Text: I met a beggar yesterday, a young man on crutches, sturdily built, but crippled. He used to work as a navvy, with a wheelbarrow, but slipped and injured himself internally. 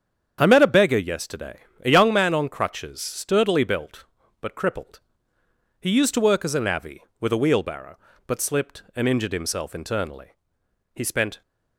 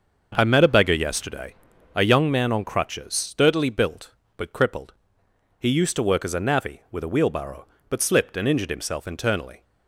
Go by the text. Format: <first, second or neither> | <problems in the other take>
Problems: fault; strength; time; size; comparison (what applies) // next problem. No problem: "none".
second | starts louder than the rest; strong; until 1.4 s; 8 dB; also in the second // goes on to say "He spent"; slight; from 10.9 s on; 0.46 s long